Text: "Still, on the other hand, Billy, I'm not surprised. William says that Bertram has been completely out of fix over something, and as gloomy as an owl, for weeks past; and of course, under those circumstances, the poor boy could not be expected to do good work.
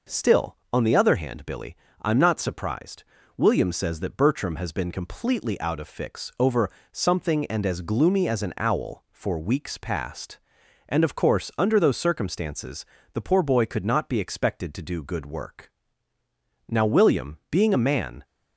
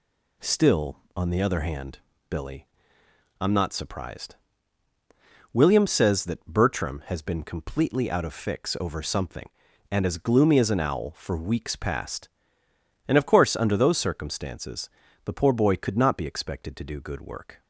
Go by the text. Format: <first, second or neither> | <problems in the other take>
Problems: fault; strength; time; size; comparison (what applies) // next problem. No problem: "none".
second | pauses between "over" and "something"; slight; at 6.7 s; 0.22 s long // goes on to say "Now William being a man"; from 16.6 s on; 1.5 s long